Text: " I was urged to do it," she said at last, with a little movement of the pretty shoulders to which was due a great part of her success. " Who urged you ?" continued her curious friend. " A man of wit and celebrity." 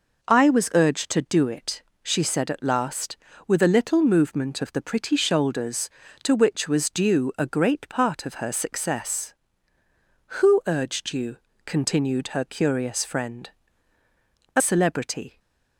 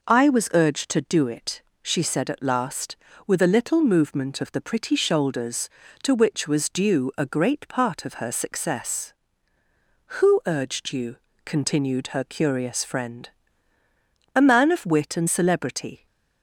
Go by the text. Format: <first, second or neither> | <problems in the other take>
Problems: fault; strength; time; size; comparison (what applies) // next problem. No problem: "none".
second | skips "man of wit and"; at 14.6 s // stays silent after the last word; slight; from 15.2 s on; 0.5 s long